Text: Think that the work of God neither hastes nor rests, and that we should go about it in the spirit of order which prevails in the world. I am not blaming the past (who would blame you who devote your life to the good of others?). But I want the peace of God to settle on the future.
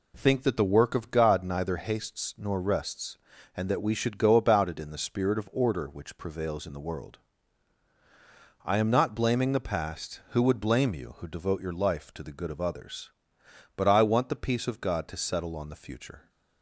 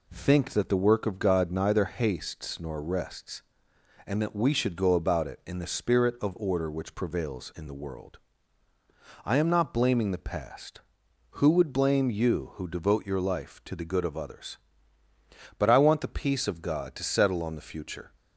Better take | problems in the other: neither | none

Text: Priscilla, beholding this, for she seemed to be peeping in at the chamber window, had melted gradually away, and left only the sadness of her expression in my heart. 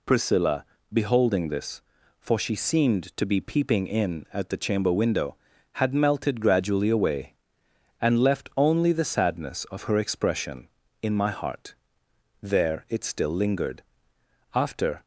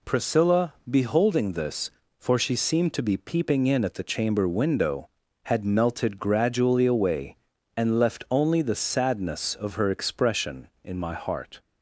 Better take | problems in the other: second | goes on to say "There it still lingered after"; strong; from 12.4 s on; 2.6 s long

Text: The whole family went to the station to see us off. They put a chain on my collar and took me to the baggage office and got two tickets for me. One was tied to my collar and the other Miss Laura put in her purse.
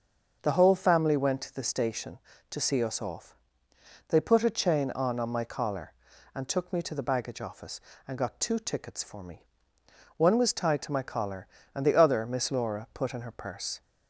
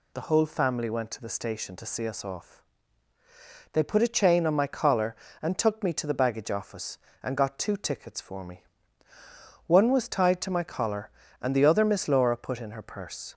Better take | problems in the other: second | starts louder than the rest; until 1.4 s; 6.5 dB // says "on" twice; at 5.1 s

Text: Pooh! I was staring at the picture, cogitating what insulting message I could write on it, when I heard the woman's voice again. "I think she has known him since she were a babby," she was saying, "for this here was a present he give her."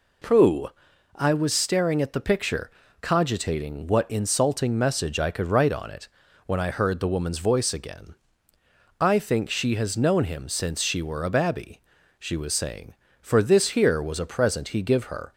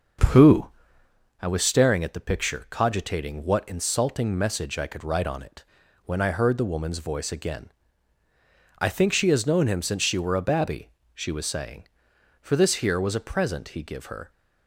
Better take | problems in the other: first | starts louder than the rest; until 1.2 s; 6.5 dB

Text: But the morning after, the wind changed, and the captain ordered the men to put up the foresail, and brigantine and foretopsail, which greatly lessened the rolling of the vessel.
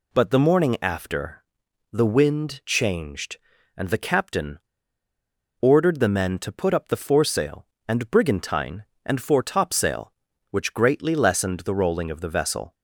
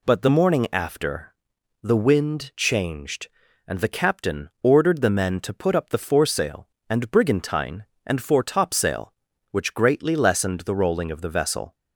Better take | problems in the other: second | pauses between "captain" and "ordered"; at 4.5 s; 1.0 s long

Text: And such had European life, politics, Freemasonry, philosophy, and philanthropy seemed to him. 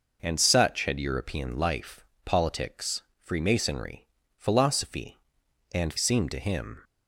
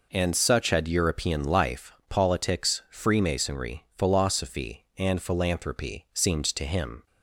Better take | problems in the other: second | skips "philanthropy"; at 5.9 s

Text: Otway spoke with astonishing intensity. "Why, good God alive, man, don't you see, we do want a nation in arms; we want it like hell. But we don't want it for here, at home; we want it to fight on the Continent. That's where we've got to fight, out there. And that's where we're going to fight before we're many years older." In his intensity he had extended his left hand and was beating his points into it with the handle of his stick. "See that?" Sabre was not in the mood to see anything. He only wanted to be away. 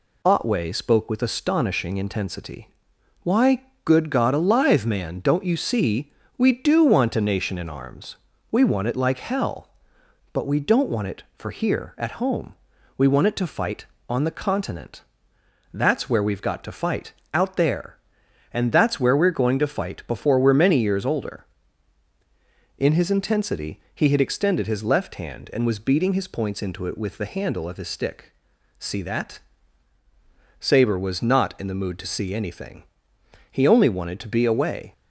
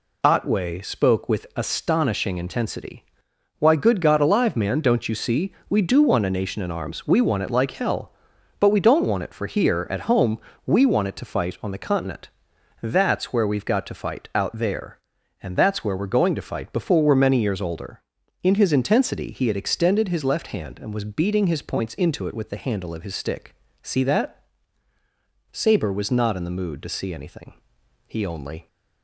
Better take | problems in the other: first | stops before "wanted to be away"; at 28.6 s

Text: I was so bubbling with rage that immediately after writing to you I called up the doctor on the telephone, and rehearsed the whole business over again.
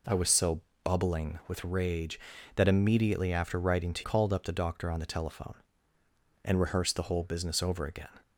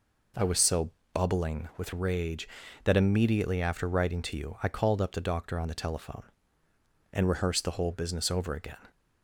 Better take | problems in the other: second | pauses between "so" and "bubbling"; slight; at 0.6 s; 0.22 s long; slight in the second // skips "you I"; at 4.0 s

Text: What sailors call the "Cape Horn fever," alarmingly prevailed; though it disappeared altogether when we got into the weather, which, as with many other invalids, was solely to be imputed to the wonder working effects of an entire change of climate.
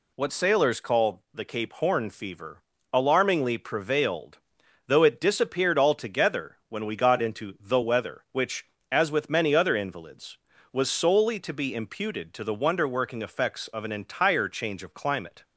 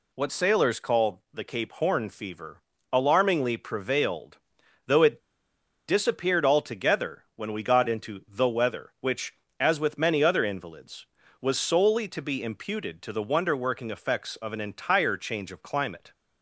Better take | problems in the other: first | pauses between "it" and "disappeared"; noticeable; at 5.2 s; 0.67 s long

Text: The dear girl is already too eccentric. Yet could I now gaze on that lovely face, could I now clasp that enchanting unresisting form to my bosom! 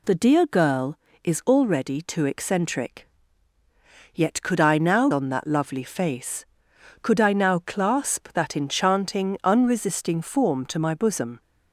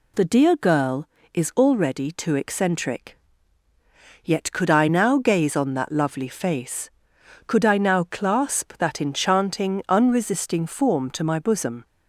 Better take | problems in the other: second | skips "gaze"; at 5.1 s

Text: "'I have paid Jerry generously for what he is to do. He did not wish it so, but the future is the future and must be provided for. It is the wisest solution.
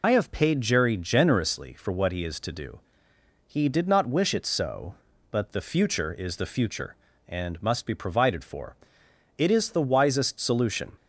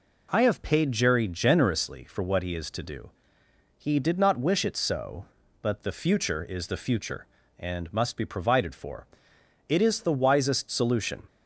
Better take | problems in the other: second | loses the start of "I"; at 0.0 s; 60 ms

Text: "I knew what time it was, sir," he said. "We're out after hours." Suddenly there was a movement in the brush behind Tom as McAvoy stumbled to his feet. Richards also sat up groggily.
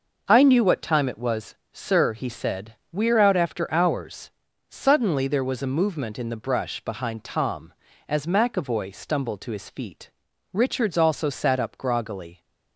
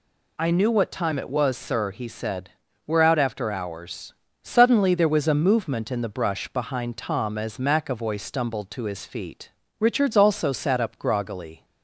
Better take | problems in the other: neither | none

